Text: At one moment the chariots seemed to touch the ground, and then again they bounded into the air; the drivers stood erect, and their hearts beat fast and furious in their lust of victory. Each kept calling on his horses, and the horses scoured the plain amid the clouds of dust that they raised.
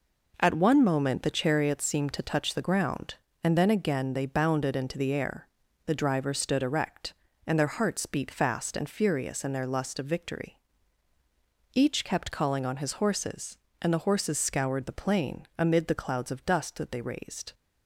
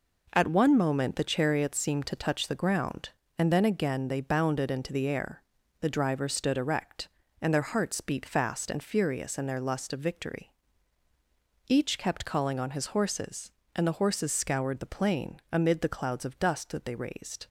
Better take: neither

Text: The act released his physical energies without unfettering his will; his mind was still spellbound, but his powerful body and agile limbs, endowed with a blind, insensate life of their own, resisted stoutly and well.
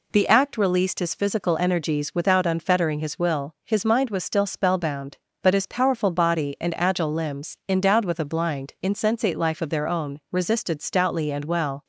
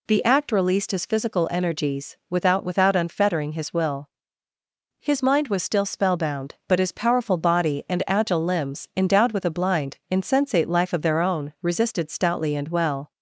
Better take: first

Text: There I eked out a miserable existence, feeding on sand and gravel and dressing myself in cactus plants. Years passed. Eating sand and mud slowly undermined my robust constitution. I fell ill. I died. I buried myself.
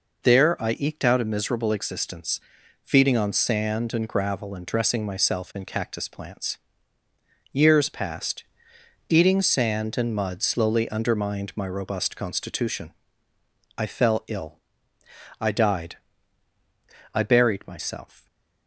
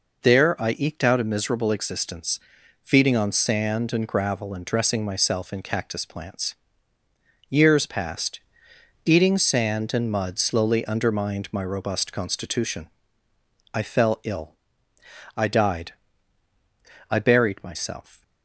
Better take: neither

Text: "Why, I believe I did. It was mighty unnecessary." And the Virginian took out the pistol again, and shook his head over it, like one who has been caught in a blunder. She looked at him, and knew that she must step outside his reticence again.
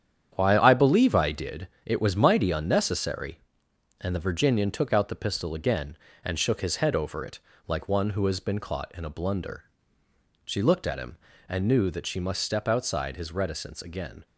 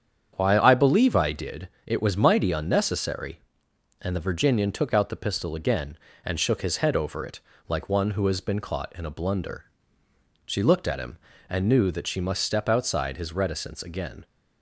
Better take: second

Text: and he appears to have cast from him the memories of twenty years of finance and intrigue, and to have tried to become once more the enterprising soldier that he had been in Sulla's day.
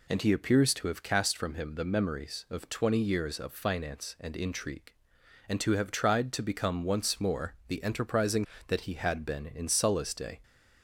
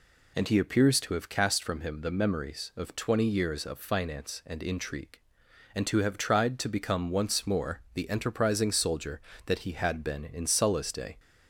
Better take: second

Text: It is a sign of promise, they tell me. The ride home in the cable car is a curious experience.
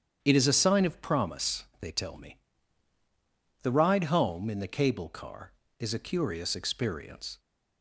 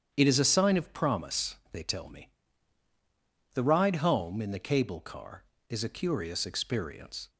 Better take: neither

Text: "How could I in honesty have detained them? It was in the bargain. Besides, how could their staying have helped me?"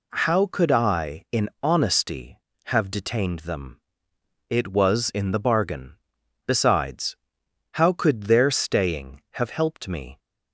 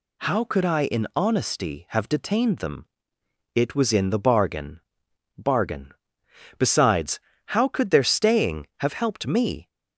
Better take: first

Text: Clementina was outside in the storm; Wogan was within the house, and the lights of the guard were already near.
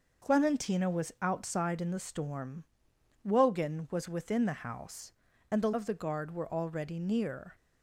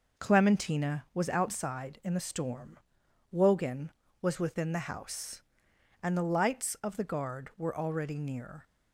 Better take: second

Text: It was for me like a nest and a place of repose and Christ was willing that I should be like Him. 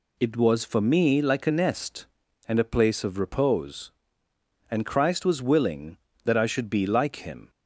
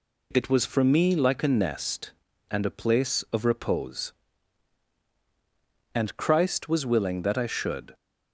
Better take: first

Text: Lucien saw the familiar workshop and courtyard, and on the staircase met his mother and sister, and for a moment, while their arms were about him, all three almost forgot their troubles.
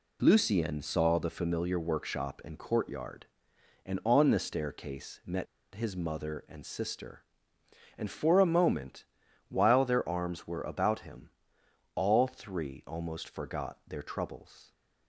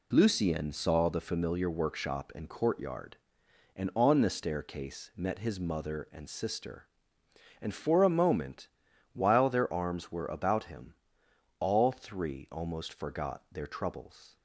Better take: second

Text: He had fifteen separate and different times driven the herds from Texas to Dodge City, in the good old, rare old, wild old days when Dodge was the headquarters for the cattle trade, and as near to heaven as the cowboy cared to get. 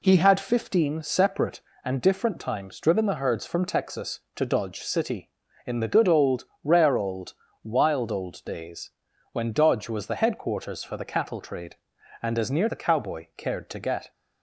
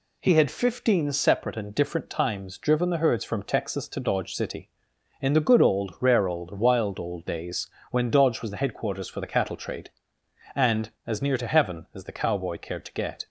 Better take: second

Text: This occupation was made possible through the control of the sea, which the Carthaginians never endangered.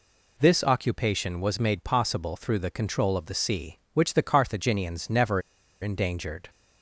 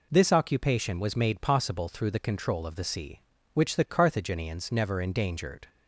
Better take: second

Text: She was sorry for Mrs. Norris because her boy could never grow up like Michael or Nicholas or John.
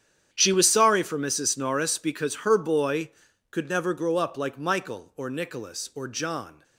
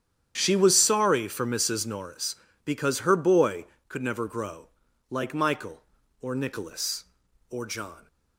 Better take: first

